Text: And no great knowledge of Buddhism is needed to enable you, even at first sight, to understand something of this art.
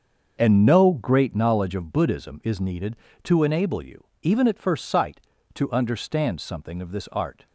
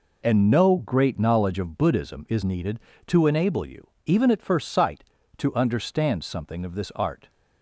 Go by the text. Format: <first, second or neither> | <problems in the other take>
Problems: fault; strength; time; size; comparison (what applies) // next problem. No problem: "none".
second | starts louder than the rest; until 1.3 s; 6.5 dB